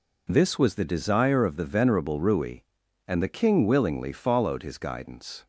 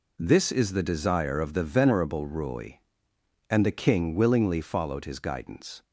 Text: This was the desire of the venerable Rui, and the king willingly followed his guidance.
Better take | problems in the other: first | says "is" for "was"; at 0.5 s

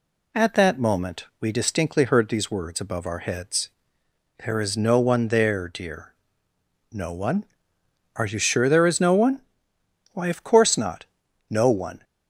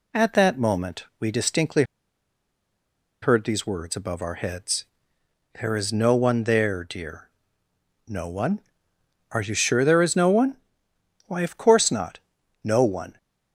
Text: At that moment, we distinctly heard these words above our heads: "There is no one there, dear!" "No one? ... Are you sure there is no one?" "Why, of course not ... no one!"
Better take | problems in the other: first | pauses between "distinctly" and "heard"; strong; at 1.8 s; 1.3 s long

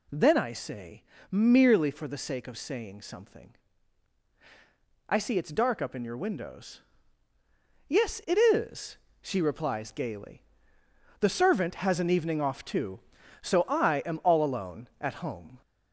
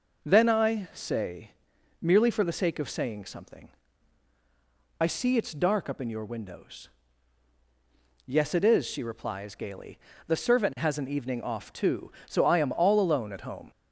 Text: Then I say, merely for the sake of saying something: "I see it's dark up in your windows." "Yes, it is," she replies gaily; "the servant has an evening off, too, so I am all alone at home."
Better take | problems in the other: second | gets louder; slight; throughout; 2.5 dB

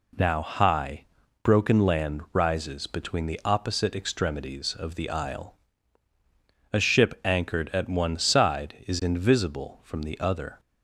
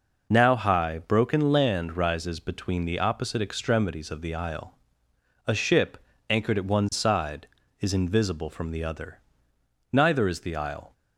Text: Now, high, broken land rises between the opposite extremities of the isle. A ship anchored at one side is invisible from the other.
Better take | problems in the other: first | pauses between "ship" and "anchored"; slight; at 5.9 s; 0.32 s long // goes on to say "Neither is the isle"; noticeable; from 9.9 s on; 1.0 s long

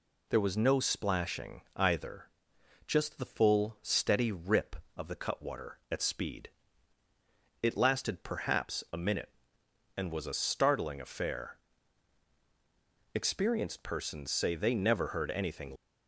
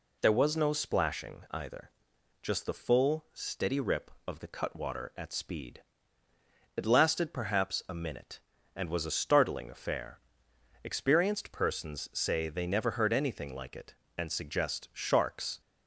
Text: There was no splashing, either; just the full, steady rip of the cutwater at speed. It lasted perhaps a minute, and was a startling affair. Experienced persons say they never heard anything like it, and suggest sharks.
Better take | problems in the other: second | stops before "like it and suggest sharks"; at 15.7 s

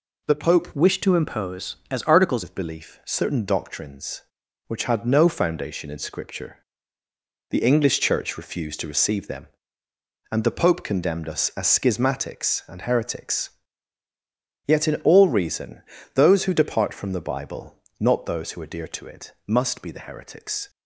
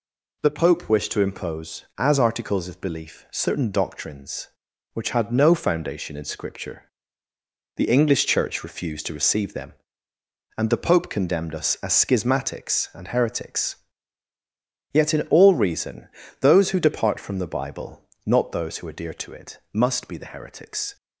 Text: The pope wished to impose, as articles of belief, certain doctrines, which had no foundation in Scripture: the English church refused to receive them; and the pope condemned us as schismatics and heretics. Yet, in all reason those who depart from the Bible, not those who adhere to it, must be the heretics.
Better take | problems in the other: second | changes voice from "wished" to "articles"; from 0.7 to 2.4 s; 1.7 s long // pauses between "reason" and "those"; slight; at 15.8 s; 0.32 s long; slight in the second

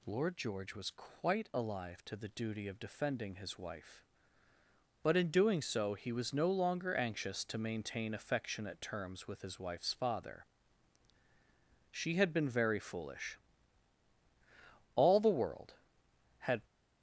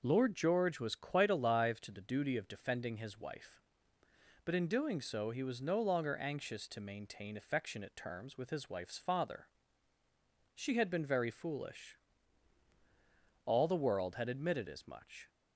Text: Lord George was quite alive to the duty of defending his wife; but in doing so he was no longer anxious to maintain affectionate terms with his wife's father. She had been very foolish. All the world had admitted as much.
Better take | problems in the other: second | stops before "admitted as much"; at 16.6 s

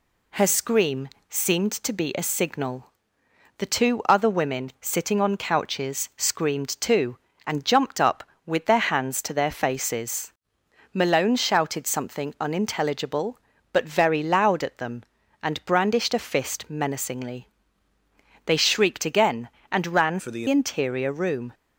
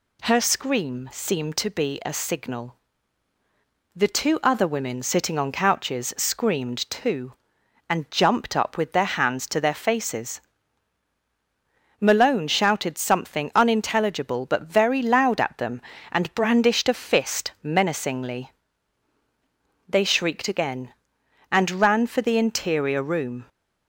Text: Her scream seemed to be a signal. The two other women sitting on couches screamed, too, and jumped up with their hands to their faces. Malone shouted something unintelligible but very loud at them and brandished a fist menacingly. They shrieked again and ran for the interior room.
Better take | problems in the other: second | pauses between "scream" and "seemed"; slight; at 1.0 s; 0.20 s long // changes voice from "for" to "the"; from 20.1 to 20.4 s; 0.3 s long

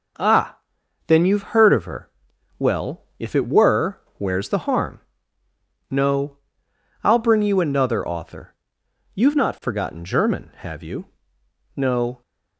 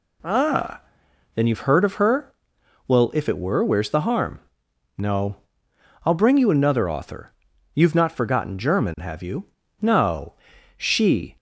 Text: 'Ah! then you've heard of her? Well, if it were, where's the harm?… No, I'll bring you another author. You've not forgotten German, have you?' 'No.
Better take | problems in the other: first | goes on to say "She"; from 10.7 s on; 0.58 s long

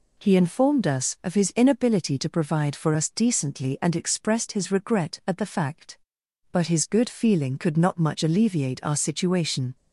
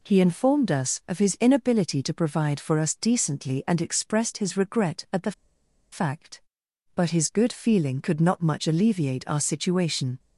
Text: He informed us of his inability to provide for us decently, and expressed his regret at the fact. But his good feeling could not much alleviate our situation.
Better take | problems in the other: first | pauses between "the" and "fact"; noticeable; at 5.3 s; 0.60 s long

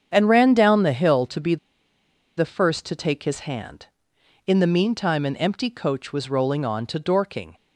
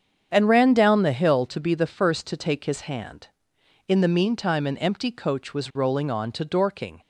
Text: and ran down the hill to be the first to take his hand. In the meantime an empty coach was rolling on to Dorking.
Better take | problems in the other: second | starts louder than the rest; strong; until 1.1 s; 8 dB; strong in the second // pauses between "be" and "the"; noticeable; at 1.5 s; 0.83 s long

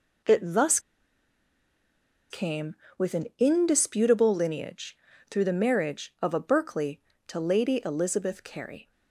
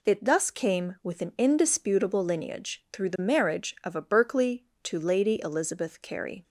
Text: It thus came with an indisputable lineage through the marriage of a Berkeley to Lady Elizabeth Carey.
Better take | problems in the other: second | pauses between "thus" and "came"; strong; at 0.7 s; 1.5 s long // pauses between "lineage" and "through"; slight; at 4.9 s; 0.32 s long

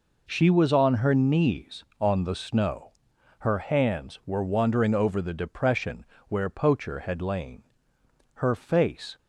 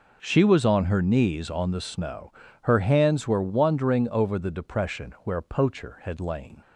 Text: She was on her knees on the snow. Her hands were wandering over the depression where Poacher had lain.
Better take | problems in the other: second | pauses between "depression" and "where"; slight; at 6.0 s; 0.24 s long // goes on to say "Her face"; noticeable; from 8.3 s on; 0.84 s long

